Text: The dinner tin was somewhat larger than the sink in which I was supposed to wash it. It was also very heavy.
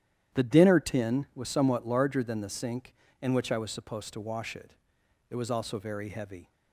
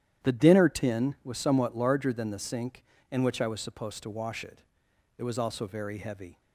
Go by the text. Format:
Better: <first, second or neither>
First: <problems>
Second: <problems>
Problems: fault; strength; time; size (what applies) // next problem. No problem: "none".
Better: neither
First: starts louder than the rest; strong; until 1.4 s; 11 dB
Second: starts louder than the rest; strong; until 1.3 s; 11 dB